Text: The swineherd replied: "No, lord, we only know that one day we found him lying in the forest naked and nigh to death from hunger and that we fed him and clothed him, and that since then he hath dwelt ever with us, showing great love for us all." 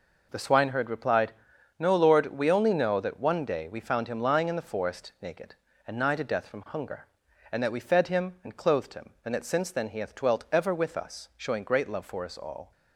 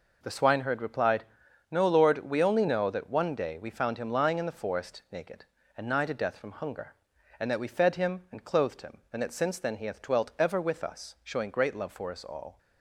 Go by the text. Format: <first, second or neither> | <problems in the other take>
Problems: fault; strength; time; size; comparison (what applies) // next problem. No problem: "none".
neither | none